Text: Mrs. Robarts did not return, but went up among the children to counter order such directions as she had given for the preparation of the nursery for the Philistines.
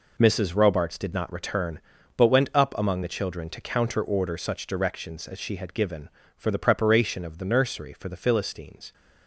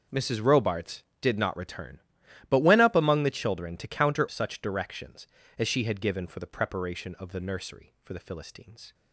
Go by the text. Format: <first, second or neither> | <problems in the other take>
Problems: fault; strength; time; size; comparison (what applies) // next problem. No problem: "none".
first | skips "order"; at 4.2 s